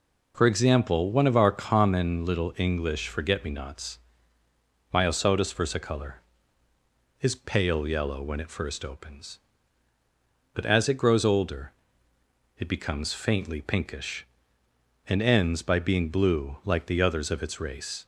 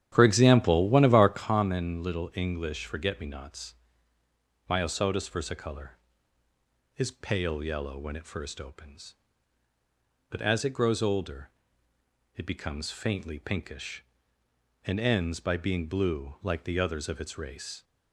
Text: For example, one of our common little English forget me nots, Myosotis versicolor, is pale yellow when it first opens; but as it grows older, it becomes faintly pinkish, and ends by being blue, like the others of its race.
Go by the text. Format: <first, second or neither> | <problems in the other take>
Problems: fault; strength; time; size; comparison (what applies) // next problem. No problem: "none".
first | starts louder than the rest; strong; until 1.5 s; 10 dB